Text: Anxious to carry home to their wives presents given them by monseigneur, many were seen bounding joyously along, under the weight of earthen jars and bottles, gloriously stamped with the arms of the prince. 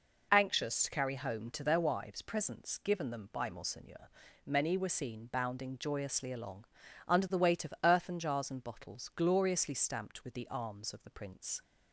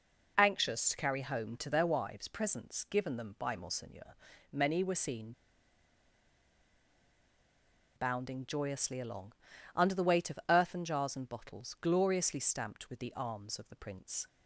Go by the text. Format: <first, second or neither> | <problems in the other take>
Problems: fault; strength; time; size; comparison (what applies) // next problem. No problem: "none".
first | pauses between "seen" and "bounding"; strong; at 5.3 s; 2.6 s long